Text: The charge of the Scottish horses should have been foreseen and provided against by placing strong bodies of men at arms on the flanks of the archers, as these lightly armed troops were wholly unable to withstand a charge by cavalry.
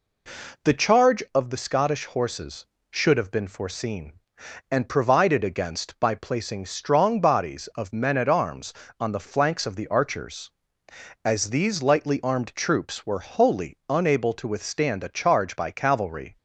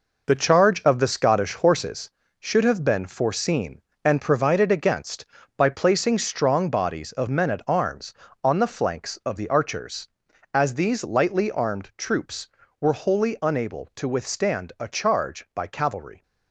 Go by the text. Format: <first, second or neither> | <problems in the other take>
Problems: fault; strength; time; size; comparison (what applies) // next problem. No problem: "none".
first | gets quieter; strong; throughout; 8 dB